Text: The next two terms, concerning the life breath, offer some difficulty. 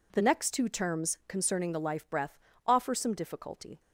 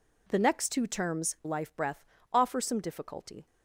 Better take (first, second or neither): first